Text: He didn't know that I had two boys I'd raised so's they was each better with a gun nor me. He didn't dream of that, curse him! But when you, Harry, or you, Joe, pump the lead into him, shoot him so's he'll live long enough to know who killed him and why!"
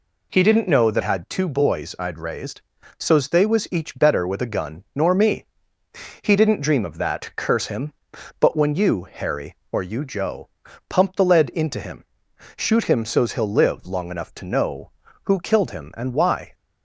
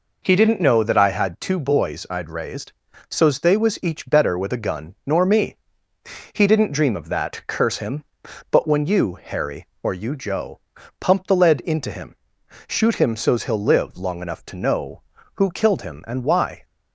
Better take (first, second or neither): second